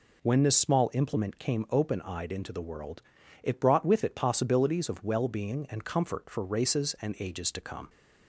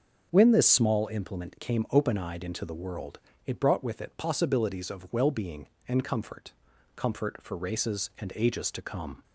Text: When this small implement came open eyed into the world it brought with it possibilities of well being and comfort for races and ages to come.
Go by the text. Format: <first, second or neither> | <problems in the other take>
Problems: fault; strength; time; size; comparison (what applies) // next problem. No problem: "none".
first | starts louder than the rest; until 1.3 s; 6.5 dB // pauses between "world" and "it"; slight; at 3.1 s; 0.30 s long; also in the first // says "comfort" twice; at 6.9 s